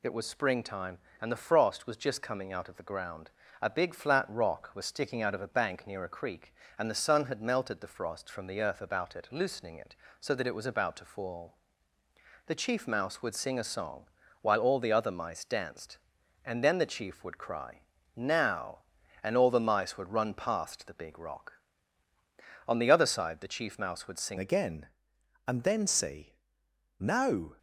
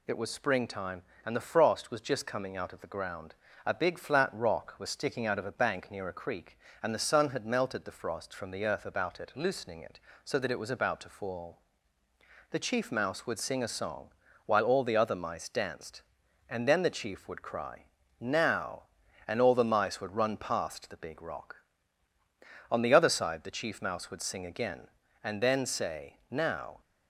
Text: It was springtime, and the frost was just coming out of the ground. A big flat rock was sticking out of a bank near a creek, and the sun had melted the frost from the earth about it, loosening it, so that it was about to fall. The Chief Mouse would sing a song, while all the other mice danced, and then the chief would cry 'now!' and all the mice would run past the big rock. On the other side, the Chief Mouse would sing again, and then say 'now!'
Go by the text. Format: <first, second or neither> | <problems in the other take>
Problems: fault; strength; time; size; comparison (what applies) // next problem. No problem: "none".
second | pauses between "cry" and "now"; slight; at 17.8 s; 0.34 s long; slight in the second // changes voice at "again"; from 24.3 s on; 3.2 s long // pauses between "say" and "now"; noticeable; at 26.3 s; 0.64 s long